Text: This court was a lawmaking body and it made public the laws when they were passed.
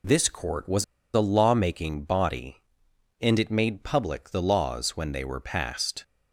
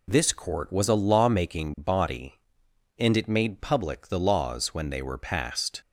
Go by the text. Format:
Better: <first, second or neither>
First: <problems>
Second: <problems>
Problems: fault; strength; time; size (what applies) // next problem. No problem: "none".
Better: second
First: pauses between "was" and "a"; slight; at 0.8 s; 0.30 s long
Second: none